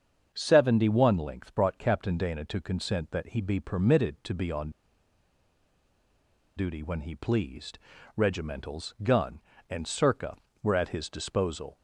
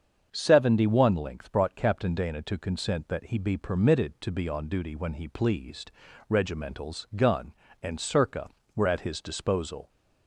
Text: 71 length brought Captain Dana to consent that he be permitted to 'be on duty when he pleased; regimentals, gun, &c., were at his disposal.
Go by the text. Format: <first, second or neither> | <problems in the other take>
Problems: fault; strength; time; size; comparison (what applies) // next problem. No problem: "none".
second | starts louder than the rest; until 1.3 s; 7 dB; also in the second // pauses between "on" and "duty"; strong; at 4.6 s; 1.8 s long